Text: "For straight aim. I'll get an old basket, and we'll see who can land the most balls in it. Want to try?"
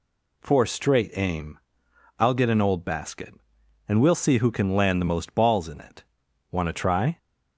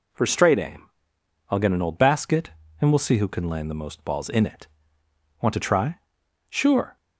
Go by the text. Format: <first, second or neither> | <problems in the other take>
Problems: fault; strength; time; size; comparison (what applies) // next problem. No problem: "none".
first | goes on to say "Sure"; slight; from 6.4 s on; 0.48 s long